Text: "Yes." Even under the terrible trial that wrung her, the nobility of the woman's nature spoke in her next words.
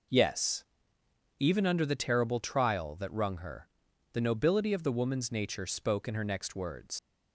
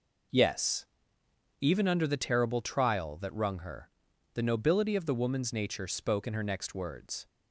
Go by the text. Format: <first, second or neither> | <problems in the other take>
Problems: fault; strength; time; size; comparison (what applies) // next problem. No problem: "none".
second | leaves "words" unfinished; at 6.9 s; 85 ms